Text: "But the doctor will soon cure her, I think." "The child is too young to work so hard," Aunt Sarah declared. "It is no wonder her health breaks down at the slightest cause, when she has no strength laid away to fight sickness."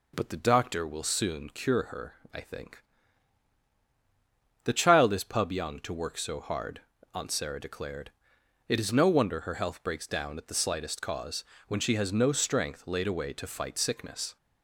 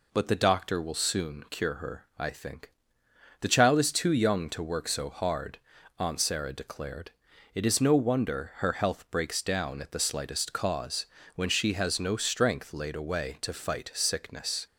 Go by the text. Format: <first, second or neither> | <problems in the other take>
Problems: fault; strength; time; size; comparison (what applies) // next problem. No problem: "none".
second | says "pub" for "too"; at 5.2 s